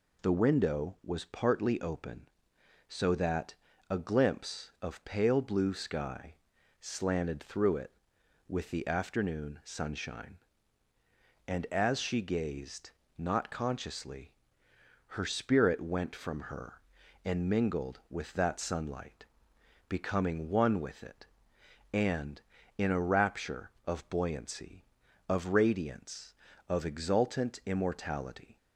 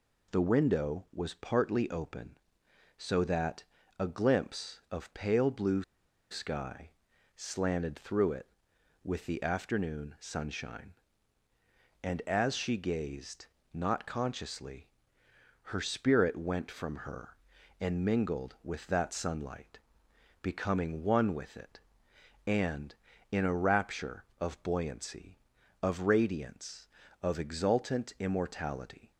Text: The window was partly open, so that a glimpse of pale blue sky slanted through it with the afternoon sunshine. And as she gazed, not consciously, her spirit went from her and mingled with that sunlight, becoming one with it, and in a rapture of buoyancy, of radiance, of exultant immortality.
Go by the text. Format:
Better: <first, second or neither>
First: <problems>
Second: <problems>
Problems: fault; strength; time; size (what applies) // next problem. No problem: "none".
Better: first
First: pauses between "that" and "a"; slight; at 3.5 s; 0.34 s long // pauses between "sky" and "slanted"; noticeable; at 6.3 s; 0.46 s long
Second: pauses between "that" and "a"; slight; at 3.6 s; 0.34 s long // pauses between "blue" and "sky"; noticeable; at 5.8 s; 0.48 s long // pauses between "sky" and "slanted"; noticeable; at 6.9 s; 0.46 s long